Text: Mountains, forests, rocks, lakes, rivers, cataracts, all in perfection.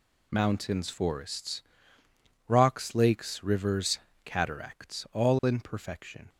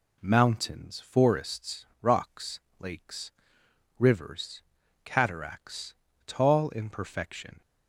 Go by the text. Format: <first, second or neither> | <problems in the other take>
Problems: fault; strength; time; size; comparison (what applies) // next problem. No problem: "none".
first | says "tall" for "all"; at 6.2 s